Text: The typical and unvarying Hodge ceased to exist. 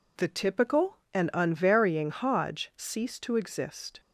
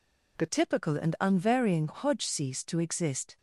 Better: first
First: none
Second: changes voice at "typical"; from 0.4 s on; 2.9 s long

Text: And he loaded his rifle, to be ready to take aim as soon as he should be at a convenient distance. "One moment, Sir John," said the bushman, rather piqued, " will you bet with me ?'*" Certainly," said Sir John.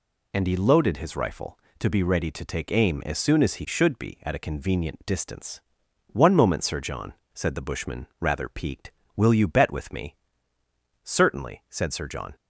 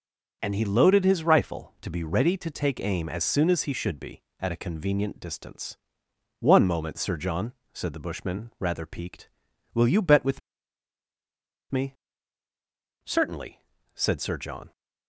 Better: first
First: none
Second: starts louder than the rest; until 1.4 s; 6.5 dB // pauses between "with" and "me"; strong; at 10.4 s; 1.3 s long

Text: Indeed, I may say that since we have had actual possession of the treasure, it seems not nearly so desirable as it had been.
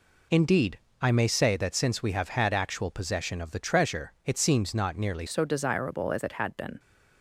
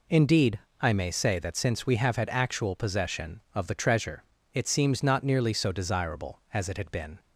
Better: second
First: changes voice at "so"; from 5.2 s on; 1.5 s long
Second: none

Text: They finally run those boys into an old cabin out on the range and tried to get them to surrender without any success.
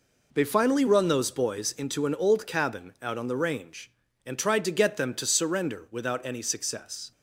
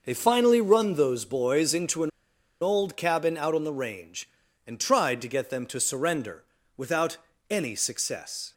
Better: first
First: none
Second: pauses between "an" and "old"; noticeable; at 2.0 s; 0.51 s long // pauses between "surrender" and "without"; slight; at 6.4 s; 0.34 s long // pauses between "without" and "any"; slight; at 7.1 s; 0.32 s long

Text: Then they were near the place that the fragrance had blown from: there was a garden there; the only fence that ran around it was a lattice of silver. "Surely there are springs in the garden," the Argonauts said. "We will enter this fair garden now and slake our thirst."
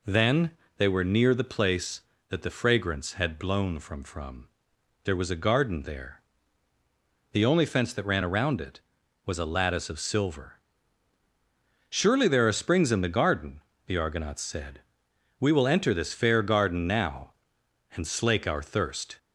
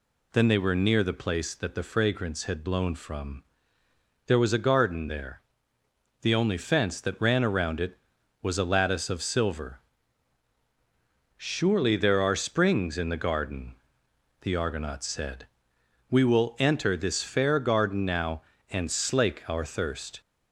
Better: second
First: pauses between "Then" and "they"; slight; at 0.5 s; 0.28 s long // says "from" twice; at 4.0 s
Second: none

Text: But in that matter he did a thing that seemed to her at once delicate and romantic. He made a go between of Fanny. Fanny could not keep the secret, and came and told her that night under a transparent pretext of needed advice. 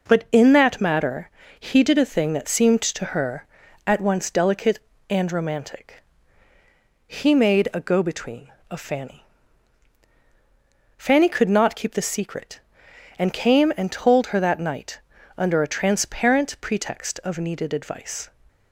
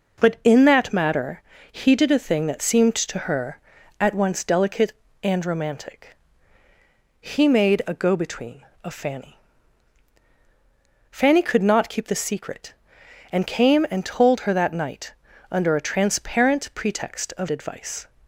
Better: first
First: pauses between "matter" and "he"; slight; at 1.2 s; 0.30 s long // pauses between "night" and "under"; at 14.9 s; 0.38 s long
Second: pauses between "matter" and "he"; slight; at 1.4 s; 0.30 s long // pauses between "night" and "under"; at 15.1 s; 0.38 s long // skips "needed"; at 17.4 s

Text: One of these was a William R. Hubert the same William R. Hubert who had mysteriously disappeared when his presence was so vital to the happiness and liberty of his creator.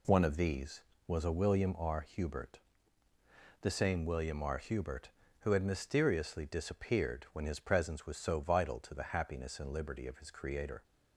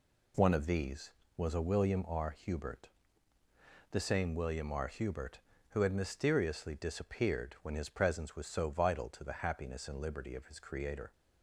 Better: neither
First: pauses between "Hubert" and "the"; at 2.5 s; 1.0 s long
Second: pauses between "Hubert" and "the"; at 2.8 s; 1.0 s long

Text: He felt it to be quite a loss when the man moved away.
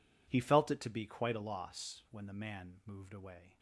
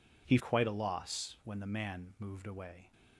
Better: first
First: none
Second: skips "felt it to be"; at 0.3 s

